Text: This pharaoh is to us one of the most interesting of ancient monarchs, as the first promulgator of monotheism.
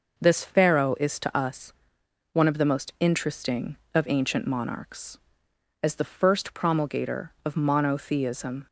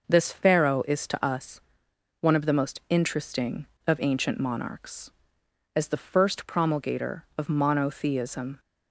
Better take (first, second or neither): neither